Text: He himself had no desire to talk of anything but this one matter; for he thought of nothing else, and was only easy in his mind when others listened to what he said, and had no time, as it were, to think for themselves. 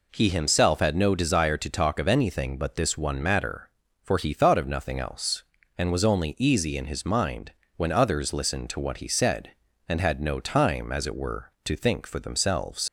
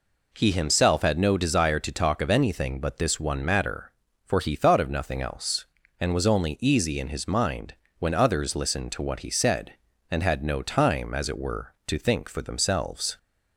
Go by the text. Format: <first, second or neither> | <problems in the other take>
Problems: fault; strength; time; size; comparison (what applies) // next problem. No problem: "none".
second | pauses between "mind" and "when"; slight; at 7.5 s; 0.24 s long; slight in the second // leaves "themselves" unfinished; at 12.8 s; 70 ms